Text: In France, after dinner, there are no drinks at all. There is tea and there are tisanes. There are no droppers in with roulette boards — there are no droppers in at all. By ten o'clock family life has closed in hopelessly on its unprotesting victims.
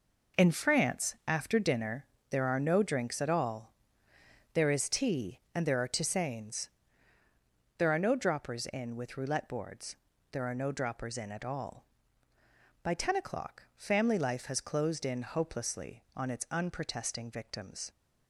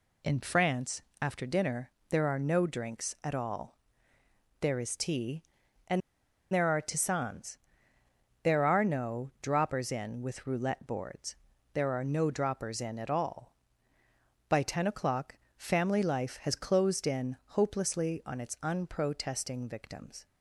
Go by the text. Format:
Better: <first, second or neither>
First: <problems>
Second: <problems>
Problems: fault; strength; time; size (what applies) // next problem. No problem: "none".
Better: first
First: none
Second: pauses between "and" and "there"; noticeable; at 6.0 s; 0.53 s long // pauses between "o'clock" and "family"; slight; at 15.3 s; 0.22 s long